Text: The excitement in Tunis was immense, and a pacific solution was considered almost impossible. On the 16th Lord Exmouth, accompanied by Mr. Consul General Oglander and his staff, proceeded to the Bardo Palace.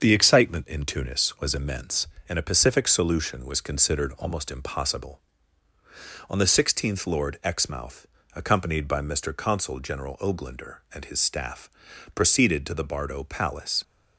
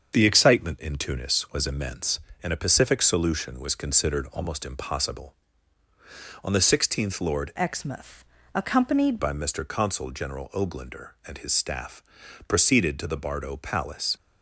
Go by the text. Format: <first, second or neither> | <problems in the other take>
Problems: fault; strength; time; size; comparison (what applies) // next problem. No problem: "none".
first | starts louder than the rest; until 1.1 s; 6.5 dB; also in the first // changes voice from "Exmouth" to "accompanied"; from 7.5 to 9.1 s; 1.6 s long